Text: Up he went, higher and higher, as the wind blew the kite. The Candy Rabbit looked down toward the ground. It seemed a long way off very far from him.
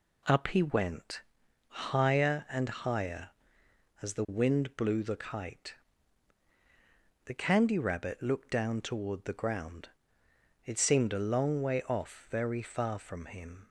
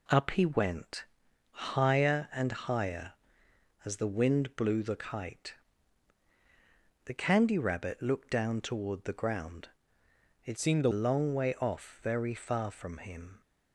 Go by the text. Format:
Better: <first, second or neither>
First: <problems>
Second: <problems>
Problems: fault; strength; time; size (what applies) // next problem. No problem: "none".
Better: first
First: none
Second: changes voice from "seemed" to "a"; from 10.5 to 10.8 s; 0.3 s long